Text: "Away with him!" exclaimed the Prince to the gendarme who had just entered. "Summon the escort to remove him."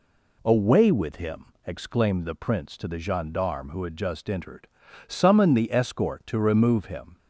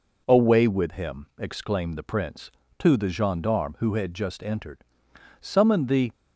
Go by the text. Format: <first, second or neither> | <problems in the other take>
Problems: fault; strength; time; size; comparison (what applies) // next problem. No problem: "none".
first | stops before "escort to remove him"; at 6.1 s